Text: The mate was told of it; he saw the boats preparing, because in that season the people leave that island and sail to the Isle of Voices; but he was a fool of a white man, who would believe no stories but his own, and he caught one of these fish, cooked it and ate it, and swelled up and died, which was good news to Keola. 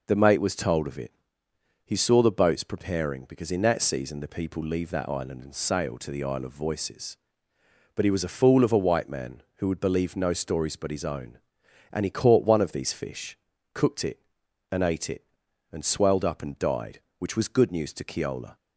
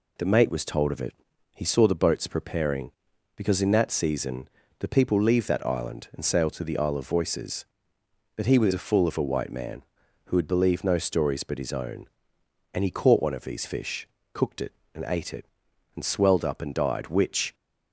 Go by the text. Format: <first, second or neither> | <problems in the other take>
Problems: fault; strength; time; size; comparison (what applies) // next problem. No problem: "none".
first | pauses between "season" and "the"; slight; at 4.4 s; 0.30 s long // stops before "was good news to Keola"; at 17.5 s